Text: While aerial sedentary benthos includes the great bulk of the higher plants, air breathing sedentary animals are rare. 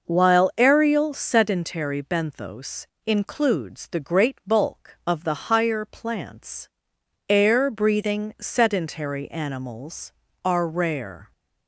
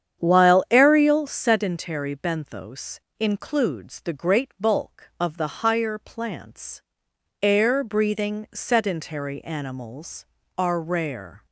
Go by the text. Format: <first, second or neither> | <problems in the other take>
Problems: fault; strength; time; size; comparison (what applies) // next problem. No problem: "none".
first | starts louder than the rest; strong; until 1.3 s; 8.5 dB // pauses between "benthos" and "includes"; slight; at 2.9 s; 0.20 s long; slight in the first